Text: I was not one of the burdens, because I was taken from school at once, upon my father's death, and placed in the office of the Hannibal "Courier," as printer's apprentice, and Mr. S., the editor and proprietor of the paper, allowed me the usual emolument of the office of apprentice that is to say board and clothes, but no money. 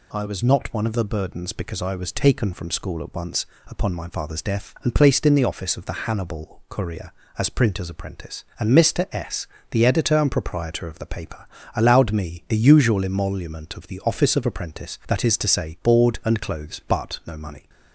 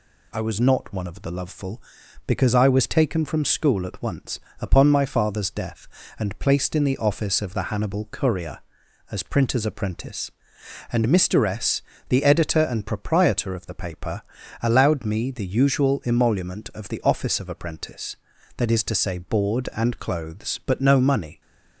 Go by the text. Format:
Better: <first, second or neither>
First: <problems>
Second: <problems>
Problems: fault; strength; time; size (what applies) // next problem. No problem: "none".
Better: first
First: none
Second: says "loveful" for "burdens"; at 1.3 s